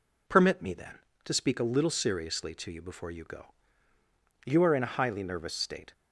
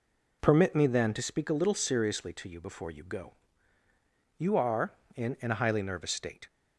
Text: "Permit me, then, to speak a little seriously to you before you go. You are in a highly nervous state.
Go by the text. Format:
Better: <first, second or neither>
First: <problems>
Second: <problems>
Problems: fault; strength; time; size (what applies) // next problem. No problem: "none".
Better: first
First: none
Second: says "in" twice; at 5.4 s